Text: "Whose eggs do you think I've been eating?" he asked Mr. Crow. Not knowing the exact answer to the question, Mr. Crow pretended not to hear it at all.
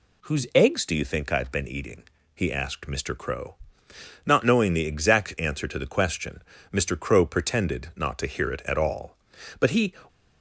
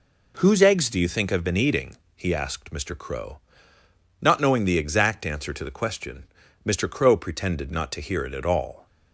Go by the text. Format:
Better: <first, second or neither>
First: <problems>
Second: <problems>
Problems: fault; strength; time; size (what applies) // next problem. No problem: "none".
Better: second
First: goes on to say "But he"; slight; from 9.5 s on; 0.36 s long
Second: none